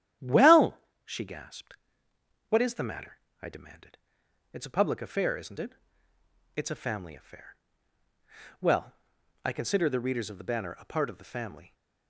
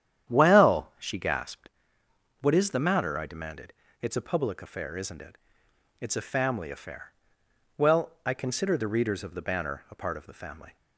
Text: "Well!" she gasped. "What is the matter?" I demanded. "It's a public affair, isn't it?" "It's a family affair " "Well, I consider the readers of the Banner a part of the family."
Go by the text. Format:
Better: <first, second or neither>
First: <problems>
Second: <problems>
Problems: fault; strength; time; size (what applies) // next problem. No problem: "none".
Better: neither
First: starts louder than the rest; strong; until 1.4 s; 11 dB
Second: starts louder than the rest; strong; until 1.3 s; 10 dB